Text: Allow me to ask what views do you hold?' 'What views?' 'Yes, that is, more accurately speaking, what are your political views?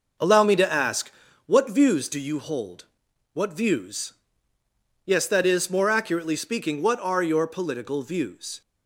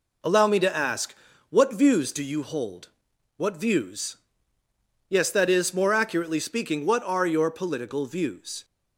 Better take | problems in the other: second | starts louder than the rest; noticeable; until 1.2 s; 5.5 dB // pauses between "ask" and "what"; slight; at 1.1 s; 0.34 s long; slight in the second

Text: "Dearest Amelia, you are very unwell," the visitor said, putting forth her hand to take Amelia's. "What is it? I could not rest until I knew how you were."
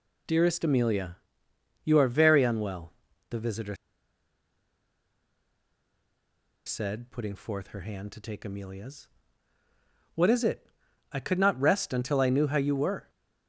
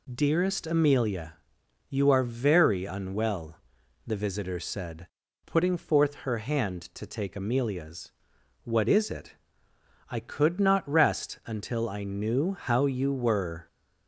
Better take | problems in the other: second | pauses between "visitor" and "said"; strong; at 3.7 s; 2.9 s long

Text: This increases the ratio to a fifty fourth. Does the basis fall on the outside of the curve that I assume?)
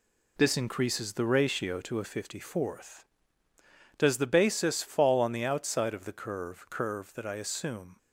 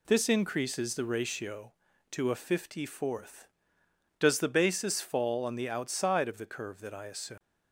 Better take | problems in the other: second | says "curve" twice; at 6.6 s

